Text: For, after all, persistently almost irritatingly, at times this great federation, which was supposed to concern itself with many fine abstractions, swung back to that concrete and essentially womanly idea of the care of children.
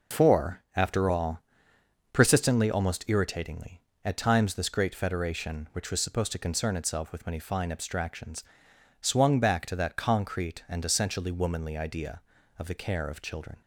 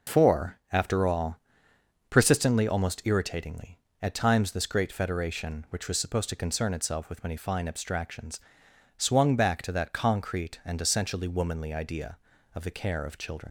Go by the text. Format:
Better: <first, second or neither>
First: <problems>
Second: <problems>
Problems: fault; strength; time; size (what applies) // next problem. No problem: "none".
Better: first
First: none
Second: leaves "children" unfinished; at 13.4 s; 70 ms